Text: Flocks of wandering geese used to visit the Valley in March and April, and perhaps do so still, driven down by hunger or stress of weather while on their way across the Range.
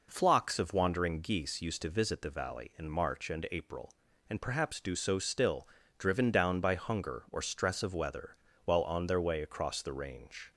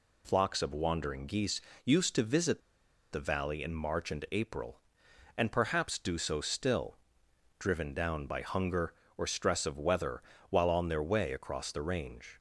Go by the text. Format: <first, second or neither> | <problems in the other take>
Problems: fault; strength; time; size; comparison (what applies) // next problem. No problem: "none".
first | pauses between "geese" and "used"; slight; at 1.5 s; 0.24 s long // pauses between "visit" and "the"; noticeable; at 2.6 s; 0.53 s long // pauses between "weather" and "while"; slight; at 10.1 s; 0.30 s long; slight in the first